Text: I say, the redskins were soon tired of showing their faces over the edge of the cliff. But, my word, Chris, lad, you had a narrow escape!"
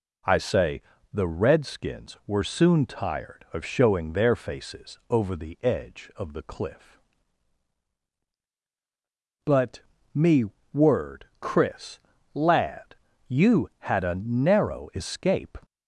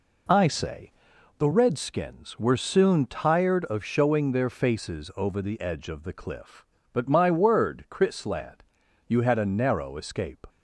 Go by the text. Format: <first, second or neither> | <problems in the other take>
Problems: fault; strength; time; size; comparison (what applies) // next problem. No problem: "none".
second | says "me" for "my"; at 10.1 s